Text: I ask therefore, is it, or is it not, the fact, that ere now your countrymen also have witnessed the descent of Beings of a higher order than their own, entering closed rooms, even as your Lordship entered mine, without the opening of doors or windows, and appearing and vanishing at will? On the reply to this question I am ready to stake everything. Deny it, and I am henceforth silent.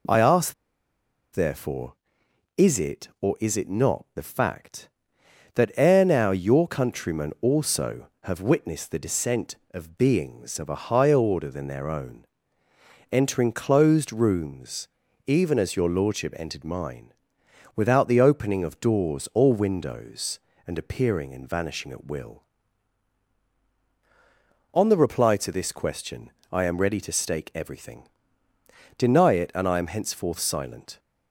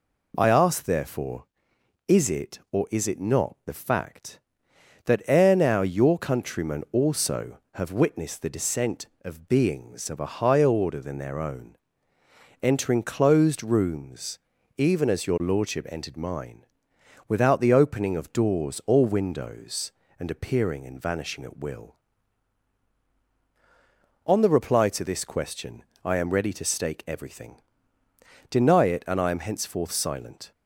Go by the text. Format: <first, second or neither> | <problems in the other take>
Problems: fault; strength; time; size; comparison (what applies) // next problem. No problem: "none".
second | pauses between "ask" and "therefore"; noticeable; at 0.5 s; 0.78 s long // pauses between "question" and "I"; slight; at 26.3 s; 0.22 s long; slight in the second